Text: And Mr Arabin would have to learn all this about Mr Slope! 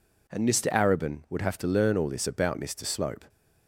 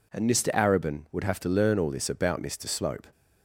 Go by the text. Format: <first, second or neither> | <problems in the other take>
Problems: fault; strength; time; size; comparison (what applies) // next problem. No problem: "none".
neither | none